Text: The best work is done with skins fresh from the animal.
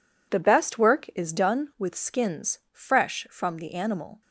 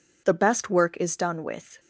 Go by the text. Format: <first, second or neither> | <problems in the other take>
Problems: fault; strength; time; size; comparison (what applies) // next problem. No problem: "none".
first | stops before "skins fresh from the animal"; at 1.7 s